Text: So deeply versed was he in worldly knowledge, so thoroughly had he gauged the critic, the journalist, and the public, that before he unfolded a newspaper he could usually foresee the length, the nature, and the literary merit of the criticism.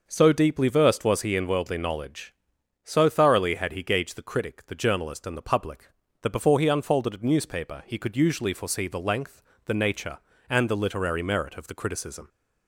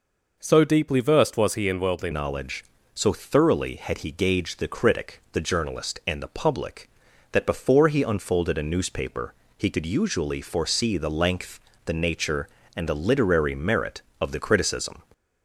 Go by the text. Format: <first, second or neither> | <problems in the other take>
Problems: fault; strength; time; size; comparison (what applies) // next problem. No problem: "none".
first | changes voice at "knowledge"; from 2.1 s on; 12.9 s long // pauses between "newspaper" and "he"; slight; at 9.3 s; 0.24 s long